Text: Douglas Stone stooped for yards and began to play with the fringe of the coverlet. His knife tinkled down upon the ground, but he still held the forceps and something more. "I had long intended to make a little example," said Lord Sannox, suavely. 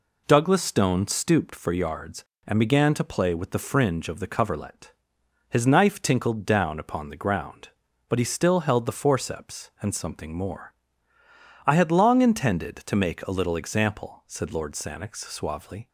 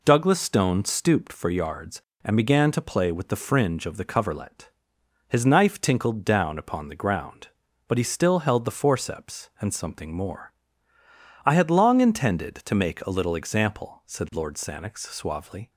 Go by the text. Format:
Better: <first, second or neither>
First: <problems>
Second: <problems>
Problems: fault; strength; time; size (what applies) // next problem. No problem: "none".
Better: neither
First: none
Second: none